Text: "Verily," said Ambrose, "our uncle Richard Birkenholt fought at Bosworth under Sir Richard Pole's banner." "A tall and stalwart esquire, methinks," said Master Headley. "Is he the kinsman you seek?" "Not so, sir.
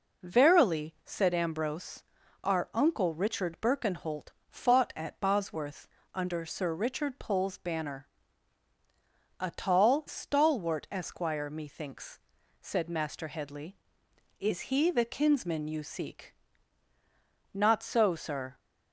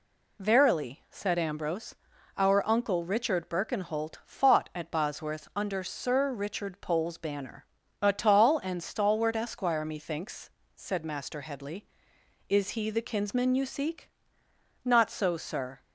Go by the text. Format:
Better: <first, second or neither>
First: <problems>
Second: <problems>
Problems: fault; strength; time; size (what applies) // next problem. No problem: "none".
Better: second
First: pauses between "Birkenholt" and "fought"; slight; at 4.3 s; 0.18 s long // pauses between "Bosworth" and "under"; slight; at 5.8 s; 0.28 s long // skips "and"; at 10.0 s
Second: none